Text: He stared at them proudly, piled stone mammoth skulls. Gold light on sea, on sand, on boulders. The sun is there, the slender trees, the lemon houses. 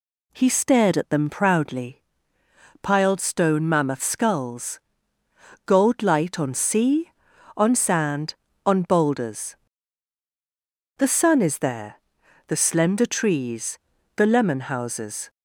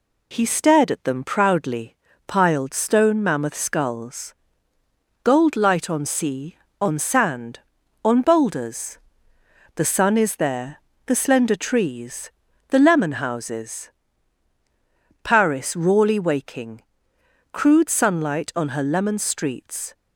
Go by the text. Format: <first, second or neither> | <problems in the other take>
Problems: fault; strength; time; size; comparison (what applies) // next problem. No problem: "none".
first | goes on to say "Paris rawly waking crude sunlight on her lemon streets"; strong; from 15.2 s on; 4.7 s long